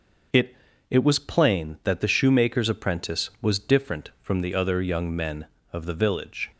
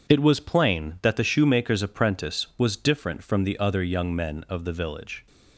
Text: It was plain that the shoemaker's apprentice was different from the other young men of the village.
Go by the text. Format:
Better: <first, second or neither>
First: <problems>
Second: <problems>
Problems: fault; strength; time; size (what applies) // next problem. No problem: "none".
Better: second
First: starts louder than the rest; noticeable; until 1.6 s; 6 dB // says "It" twice; at 0.8 s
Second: none